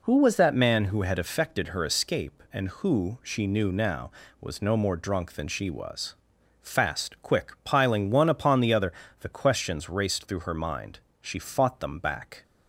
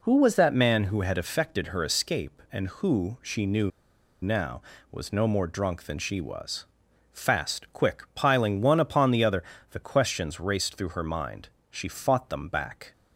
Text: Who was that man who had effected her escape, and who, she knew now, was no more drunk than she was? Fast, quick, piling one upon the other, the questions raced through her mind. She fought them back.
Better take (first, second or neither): first